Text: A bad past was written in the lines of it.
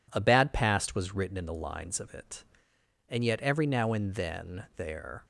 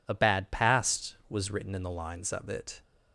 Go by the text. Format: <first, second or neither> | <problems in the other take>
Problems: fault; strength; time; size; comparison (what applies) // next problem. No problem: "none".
second | goes on to say "And yet every now and then there"; strong; from 3.0 s on; 2.1 s long